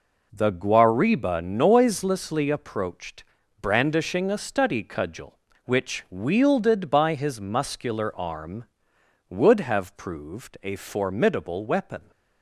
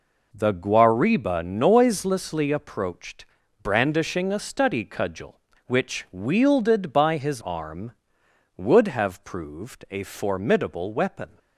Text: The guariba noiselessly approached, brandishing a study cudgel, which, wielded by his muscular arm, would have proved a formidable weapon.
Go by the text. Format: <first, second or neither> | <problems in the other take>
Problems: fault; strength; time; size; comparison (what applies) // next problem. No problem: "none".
first | skips "muscular"; at 7.4 s